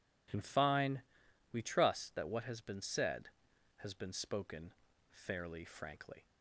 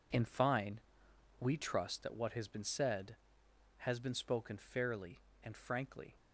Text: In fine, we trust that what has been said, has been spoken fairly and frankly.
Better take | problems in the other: second | pauses between "spoken" and "fairly"; at 4.7 s; 0.40 s long // skips "and"; at 5.6 s

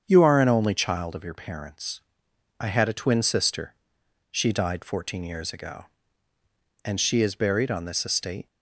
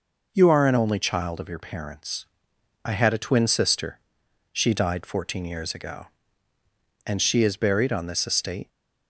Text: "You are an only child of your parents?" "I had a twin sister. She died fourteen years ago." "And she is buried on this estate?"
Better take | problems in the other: second | starts louder than the rest; strong; until 1.0 s; 7.5 dB

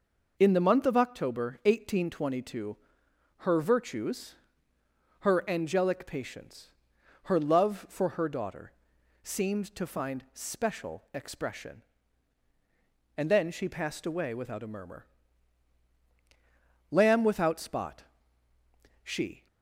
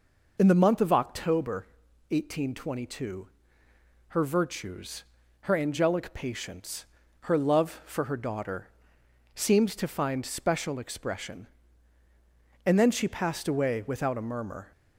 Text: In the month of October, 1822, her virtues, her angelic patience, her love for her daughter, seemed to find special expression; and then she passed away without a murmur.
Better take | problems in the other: second | goes on to say "Lamb without spot she"; strong; from 16.9 s on; 2.5 s long

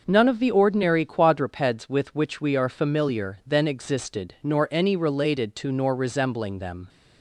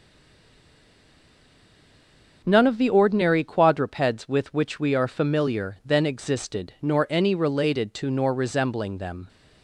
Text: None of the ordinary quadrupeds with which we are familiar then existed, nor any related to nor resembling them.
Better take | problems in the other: first | stays silent before the first word; until 2.4 s; 2.4 s long

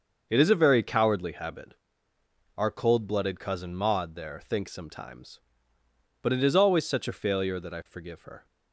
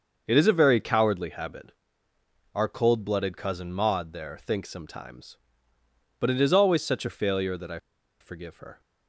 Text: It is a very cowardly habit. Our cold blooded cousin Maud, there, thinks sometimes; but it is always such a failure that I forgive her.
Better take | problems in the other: first | starts louder than the rest; until 1.2 s; 6.5 dB; also in the first // pauses between "I" and "forgive"; at 7.7 s; 0.42 s long

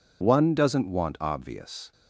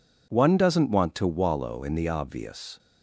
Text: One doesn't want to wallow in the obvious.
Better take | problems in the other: second | skips "to wallow in the"; at 1.1 s

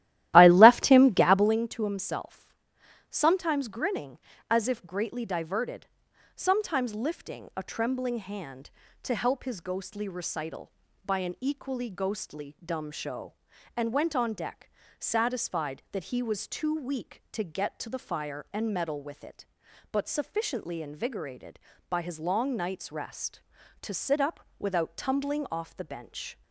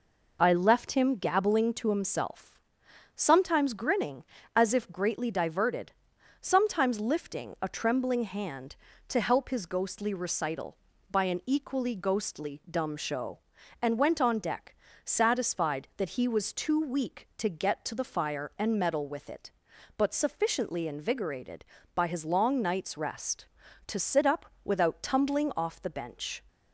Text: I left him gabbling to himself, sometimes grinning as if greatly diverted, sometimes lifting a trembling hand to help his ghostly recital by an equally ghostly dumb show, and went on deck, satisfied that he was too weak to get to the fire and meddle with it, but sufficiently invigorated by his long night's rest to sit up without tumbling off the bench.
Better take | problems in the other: second | starts louder than the rest; strong; until 1.6 s; 14.5 dB // pauses between "up" and "without"; slight; at 24.4 s; 0.18 s long; slight in the second

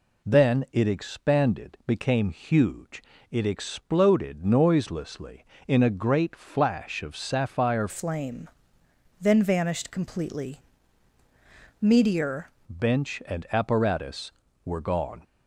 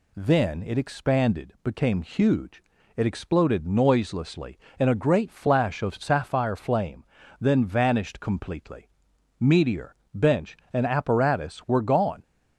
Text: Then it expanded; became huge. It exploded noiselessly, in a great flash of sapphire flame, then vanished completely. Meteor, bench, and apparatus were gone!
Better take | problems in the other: second | changes voice from "flame" to "Meteor"; from 7.8 to 12.4 s; 4.6 s long

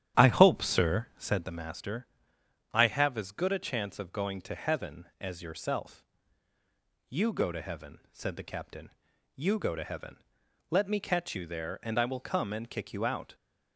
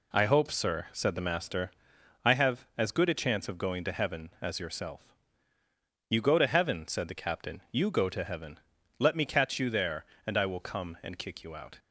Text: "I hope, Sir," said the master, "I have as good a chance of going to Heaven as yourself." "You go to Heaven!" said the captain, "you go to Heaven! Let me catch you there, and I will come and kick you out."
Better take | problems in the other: second | starts louder than the rest; strong; until 1.5 s; 10.5 dB

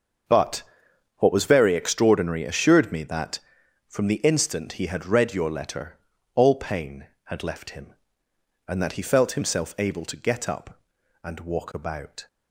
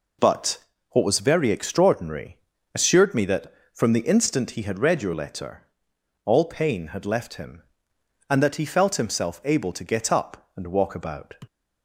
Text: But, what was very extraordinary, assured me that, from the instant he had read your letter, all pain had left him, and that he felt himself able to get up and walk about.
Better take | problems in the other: second | starts louder than the rest; until 2.0 s; 6.5 dB

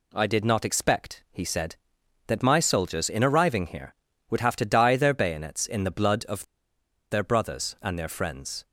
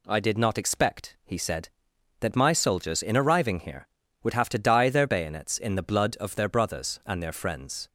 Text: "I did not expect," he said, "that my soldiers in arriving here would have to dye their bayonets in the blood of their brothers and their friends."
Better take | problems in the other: second | pauses between "of" and "their"; noticeable; at 6.4 s; 0.67 s long

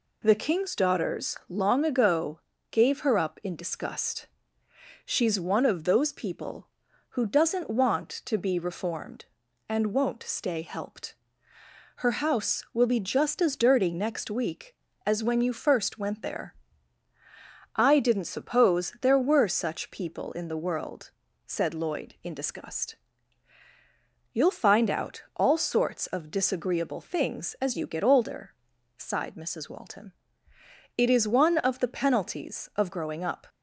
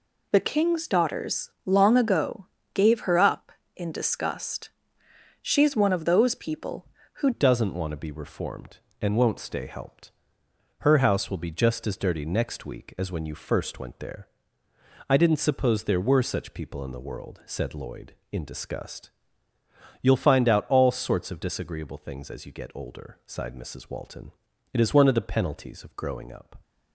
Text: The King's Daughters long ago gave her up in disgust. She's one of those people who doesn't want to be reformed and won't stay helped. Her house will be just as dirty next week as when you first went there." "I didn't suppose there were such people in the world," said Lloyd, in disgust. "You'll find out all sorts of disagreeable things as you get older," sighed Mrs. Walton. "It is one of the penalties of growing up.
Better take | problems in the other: first | pauses between "Daughters" and "long"; slight; at 1.4 s; 0.16 s long // pauses between "ago" and "gave"; slight; at 2.4 s; 0.26 s long; slight in the first // changes voice at "doesn't"; from 7.3 s on; 19.3 s long

